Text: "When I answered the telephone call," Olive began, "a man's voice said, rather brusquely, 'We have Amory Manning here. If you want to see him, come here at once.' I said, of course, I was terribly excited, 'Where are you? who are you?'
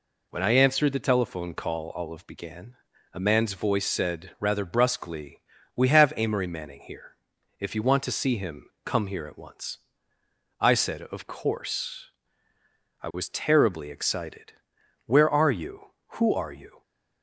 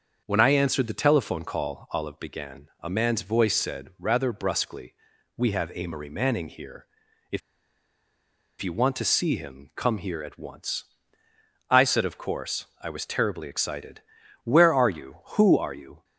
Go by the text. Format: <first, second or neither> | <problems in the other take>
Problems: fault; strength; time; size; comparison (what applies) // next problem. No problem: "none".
first | starts louder than the rest; until 1.2 s; 6.5 dB // pauses between "If" and "you"; at 7.4 s; 1.2 s long